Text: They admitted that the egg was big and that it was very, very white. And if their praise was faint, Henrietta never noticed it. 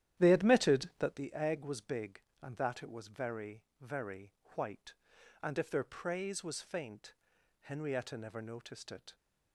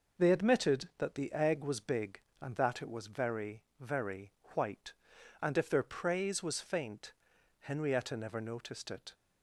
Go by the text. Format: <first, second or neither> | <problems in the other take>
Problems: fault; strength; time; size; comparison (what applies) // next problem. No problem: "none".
second | starts louder than the rest; strong; until 1.2 s; 11.5 dB // pauses between "very" and "white"; slight; at 4.3 s; 0.22 s long; slight in the second